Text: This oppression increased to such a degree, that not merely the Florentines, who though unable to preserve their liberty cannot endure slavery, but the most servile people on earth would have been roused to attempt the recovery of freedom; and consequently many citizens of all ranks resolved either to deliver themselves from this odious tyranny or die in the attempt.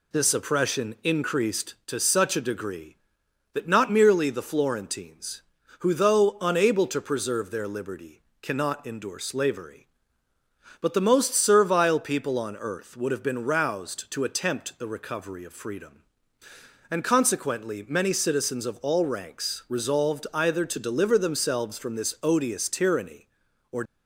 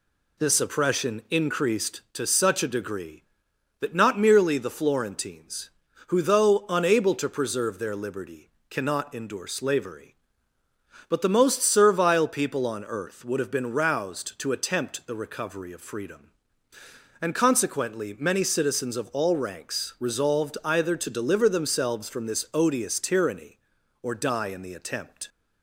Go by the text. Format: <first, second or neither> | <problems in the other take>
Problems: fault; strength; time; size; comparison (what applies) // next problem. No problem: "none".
second | pauses between "liberty" and "cannot"; slight; at 8.2 s; 0.20 s long; slight in the second // stops before "die in the attempt"; at 23.8 s